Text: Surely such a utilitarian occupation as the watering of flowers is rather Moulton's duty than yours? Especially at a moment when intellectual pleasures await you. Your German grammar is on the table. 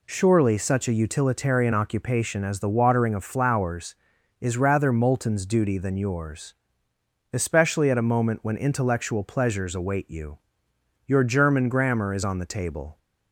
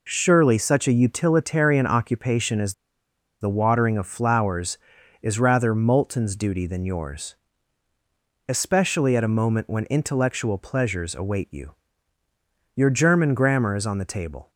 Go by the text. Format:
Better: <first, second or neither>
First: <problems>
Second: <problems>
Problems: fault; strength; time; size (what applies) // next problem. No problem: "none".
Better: first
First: none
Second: pauses between "as" and "the"; noticeable; at 2.7 s; 0.69 s long